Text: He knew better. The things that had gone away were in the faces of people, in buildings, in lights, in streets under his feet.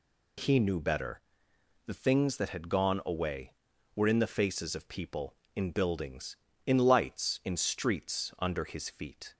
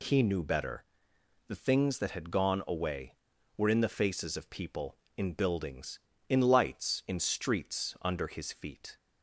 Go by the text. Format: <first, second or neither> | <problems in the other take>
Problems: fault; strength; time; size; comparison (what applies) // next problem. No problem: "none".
neither | none